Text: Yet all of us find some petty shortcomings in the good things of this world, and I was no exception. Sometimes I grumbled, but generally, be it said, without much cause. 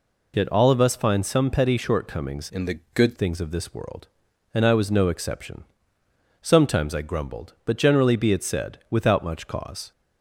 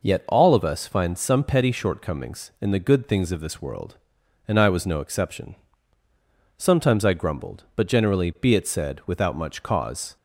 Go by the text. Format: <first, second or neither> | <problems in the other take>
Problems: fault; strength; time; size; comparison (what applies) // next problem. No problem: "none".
second | changes voice from "in" to "good"; from 2.5 to 3.1 s; 0.6 s long // pauses between "the" and "good"; slight; at 2.7 s; 0.16 s long